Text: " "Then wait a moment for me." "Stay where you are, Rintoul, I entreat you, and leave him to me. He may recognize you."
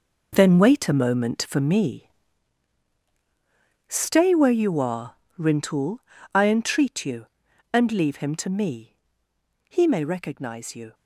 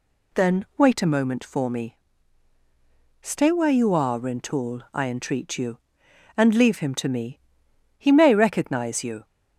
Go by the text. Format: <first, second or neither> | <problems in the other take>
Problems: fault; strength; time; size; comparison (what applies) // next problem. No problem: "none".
second | gets quieter; strong; throughout; 10.5 dB